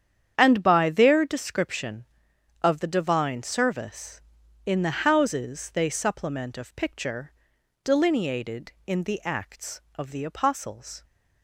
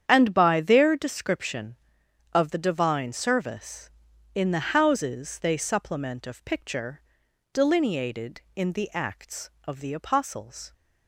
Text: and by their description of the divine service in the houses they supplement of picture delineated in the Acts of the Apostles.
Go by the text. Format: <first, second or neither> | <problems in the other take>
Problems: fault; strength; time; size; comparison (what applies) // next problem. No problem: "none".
neither | starts louder than the rest; strong; the same in both // pauses between "picture" and "delineated"; noticeable; the same in both